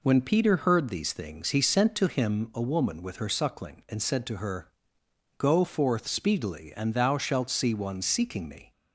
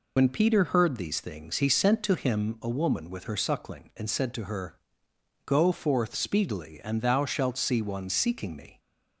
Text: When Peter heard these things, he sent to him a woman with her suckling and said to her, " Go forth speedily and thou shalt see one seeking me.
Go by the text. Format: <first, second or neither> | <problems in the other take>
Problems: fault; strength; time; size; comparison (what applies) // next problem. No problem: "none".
first | loses the start of "When"; at 0.1 s; 55 ms